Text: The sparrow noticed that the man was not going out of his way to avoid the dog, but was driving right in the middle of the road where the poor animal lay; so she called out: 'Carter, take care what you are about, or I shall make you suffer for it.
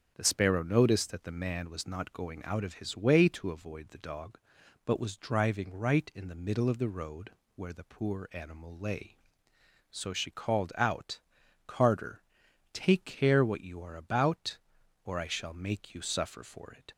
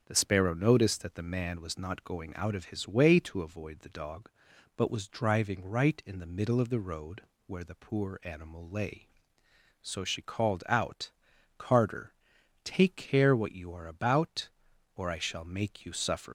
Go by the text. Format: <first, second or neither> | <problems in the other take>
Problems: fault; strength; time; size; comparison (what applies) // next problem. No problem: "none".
first | starts louder than the rest; until 1.0 s; 7 dB; also in the first // pauses between "road" and "where"; slight; at 7.2 s; 0.24 s long; slight in the first // stops before "for it"; at 16.2 s